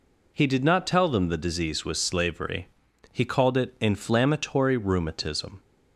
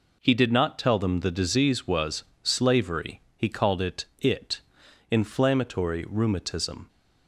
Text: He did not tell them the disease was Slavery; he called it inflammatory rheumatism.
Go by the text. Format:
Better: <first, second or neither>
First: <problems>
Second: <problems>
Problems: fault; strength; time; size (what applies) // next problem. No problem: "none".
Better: first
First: none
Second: pauses between "was" and "Slavery"; slight; at 2.2 s; 0.18 s long // says "it" twice; at 4.1 s